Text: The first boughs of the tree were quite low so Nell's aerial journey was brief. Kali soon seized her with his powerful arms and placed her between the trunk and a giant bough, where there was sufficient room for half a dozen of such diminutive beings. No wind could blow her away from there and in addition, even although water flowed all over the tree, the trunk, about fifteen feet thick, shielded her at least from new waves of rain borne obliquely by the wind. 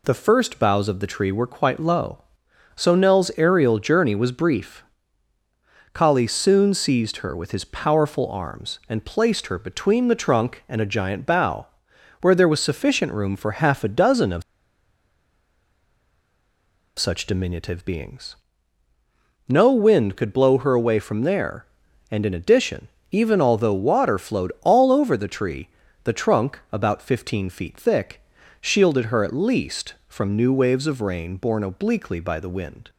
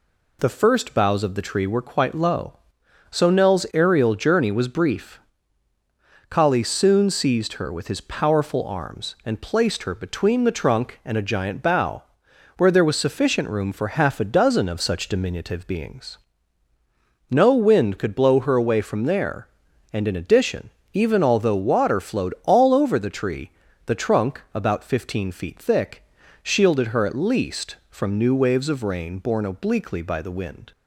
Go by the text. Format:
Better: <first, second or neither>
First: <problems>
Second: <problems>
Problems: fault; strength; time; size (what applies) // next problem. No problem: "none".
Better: second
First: pauses between "of" and "such"; strong; at 14.4 s; 2.5 s long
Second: none